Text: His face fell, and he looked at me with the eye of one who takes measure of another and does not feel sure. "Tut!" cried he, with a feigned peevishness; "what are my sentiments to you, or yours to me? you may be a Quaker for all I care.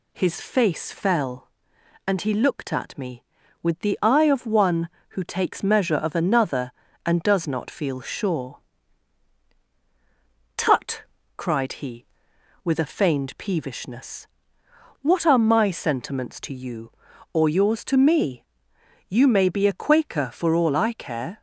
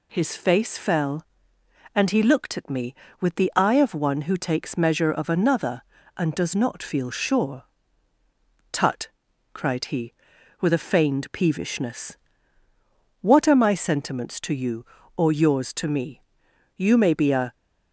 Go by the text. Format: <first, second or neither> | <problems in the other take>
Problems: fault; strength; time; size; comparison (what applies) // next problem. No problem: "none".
first | stops before "Quaker for all I care"; at 17.5 s